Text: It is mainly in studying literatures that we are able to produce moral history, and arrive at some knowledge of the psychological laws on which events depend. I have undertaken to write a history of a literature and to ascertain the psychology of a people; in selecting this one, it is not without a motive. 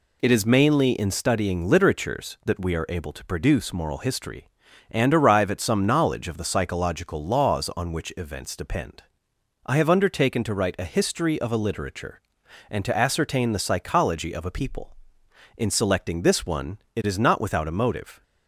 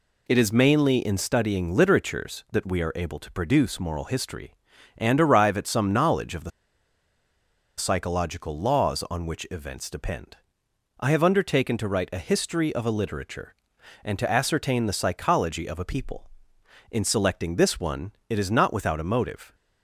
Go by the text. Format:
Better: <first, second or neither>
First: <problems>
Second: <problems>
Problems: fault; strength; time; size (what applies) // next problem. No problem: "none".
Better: first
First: none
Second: pauses between "the" and "psychological"; strong; at 6.5 s; 1.2 s long